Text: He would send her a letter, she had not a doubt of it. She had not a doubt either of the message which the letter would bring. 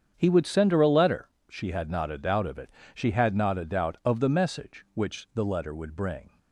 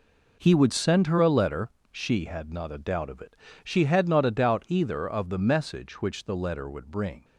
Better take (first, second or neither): second